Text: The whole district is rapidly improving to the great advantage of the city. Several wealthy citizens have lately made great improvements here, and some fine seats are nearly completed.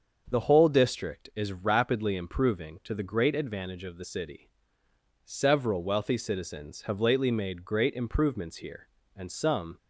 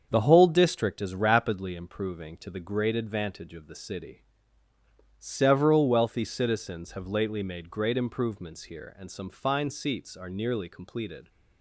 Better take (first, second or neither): second